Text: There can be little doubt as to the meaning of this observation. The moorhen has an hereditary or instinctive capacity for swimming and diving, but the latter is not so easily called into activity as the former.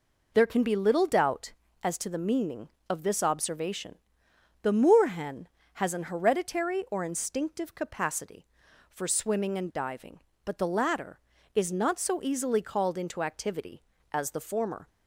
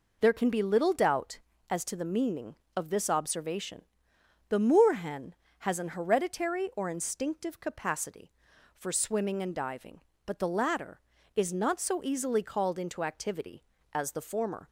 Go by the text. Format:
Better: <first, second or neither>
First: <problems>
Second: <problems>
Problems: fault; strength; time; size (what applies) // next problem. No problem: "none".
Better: neither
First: none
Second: none